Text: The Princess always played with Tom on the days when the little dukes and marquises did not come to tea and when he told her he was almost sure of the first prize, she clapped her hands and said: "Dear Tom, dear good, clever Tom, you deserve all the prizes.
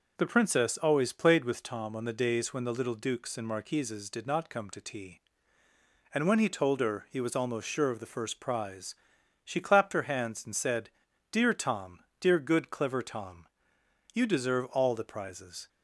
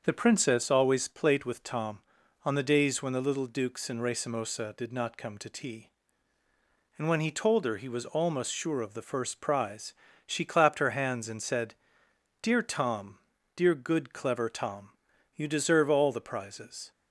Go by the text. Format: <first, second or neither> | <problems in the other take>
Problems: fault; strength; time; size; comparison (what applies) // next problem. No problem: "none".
first | starts louder than the rest; until 1.0 s; 6.5 dB // says "racemosa" for "marquises"; at 4.0 s